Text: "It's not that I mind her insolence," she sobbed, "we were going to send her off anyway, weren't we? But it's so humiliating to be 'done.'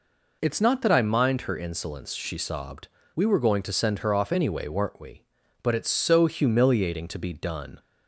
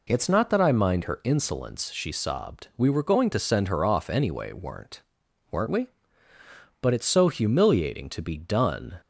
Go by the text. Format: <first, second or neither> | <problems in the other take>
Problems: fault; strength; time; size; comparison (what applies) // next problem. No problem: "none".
first | says "weren't" twice; at 5.5 s